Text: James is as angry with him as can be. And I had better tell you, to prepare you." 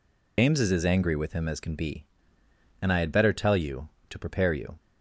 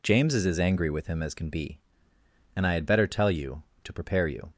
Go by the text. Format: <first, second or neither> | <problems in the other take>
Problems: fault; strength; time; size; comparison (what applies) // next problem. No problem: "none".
second | loses the start of "James"; at 0.3 s; 90 ms